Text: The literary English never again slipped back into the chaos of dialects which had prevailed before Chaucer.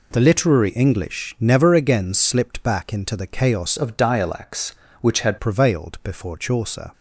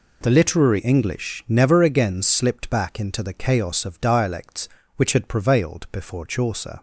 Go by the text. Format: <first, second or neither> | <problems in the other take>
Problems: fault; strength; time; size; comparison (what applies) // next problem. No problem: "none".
second | changes voice from "of" to "had"; from 3.7 to 5.3 s; 1.6 s long